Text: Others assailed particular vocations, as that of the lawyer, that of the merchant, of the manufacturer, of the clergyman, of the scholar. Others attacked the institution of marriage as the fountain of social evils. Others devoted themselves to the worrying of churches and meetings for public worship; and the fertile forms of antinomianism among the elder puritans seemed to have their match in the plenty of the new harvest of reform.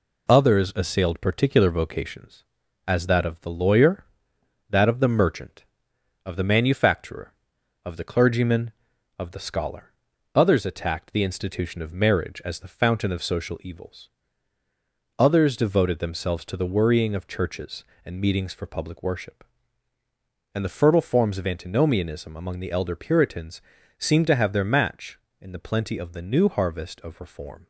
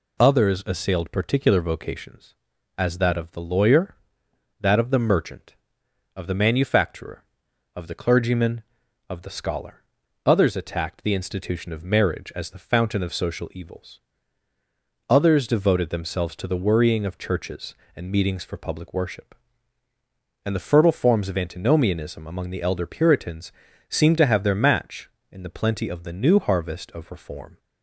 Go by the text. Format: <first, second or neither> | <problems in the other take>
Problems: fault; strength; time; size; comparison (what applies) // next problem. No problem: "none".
second | gets quieter; throughout; 4 dB // pauses between "puritans" and "seemed"; at 23.6 s; 0.38 s long; also in the second